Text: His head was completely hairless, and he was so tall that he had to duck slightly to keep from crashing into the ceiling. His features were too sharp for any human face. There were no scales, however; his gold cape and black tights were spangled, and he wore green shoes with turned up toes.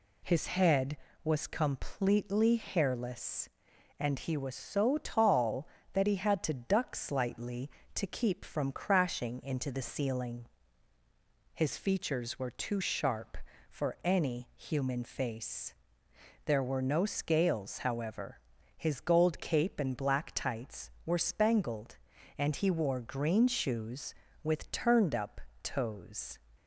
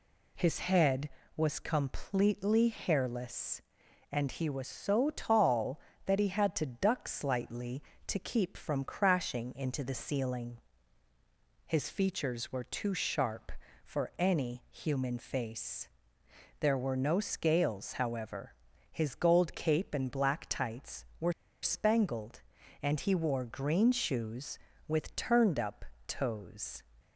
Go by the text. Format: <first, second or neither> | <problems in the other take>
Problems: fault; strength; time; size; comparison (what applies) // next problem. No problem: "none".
first | pauses between "were" and "spangled"; slight; at 21.3 s; 0.30 s long // pauses between "up" and "toes"; slight; at 25.8 s; 0.24 s long; slight in the first